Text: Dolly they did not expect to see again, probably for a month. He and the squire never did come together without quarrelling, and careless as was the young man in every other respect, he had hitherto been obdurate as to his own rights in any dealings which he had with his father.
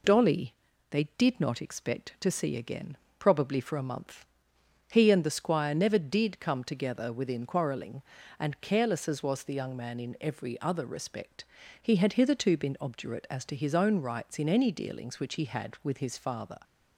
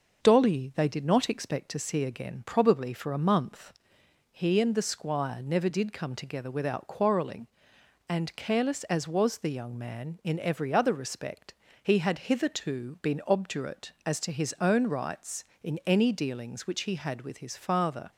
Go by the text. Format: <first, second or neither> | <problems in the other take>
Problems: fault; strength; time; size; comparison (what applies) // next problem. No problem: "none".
second | pauses between "Dolly" and "they"; at 0.5 s; 0.38 s long // says "within" for "without"; at 7.1 s